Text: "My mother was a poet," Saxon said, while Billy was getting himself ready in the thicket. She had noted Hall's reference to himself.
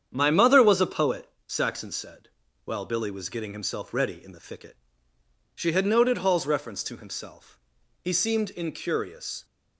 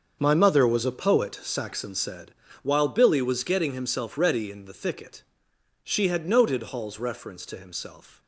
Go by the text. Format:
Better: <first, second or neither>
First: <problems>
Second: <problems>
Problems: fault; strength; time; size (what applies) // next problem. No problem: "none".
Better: second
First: starts louder than the rest; strong; until 1.1 s; 8.5 dB // goes on to say "He seemed incurious"; from 8.0 s on; 1.4 s long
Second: starts louder than the rest; until 1.2 s; 6.5 dB